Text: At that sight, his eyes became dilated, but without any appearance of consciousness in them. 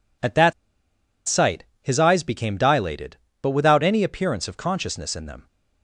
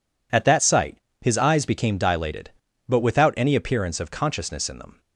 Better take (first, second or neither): second